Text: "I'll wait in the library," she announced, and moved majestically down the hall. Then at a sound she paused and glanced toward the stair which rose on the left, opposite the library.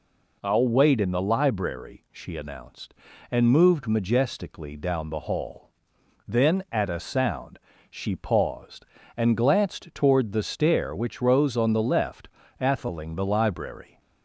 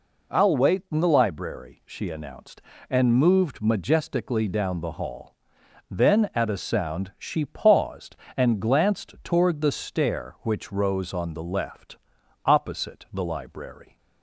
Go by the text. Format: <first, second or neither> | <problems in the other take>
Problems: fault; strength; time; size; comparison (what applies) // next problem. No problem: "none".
second | pauses between "sound" and "she"; slight; at 7.5 s; 0.32 s long // says "atheling" for "opposite"; at 12.5 s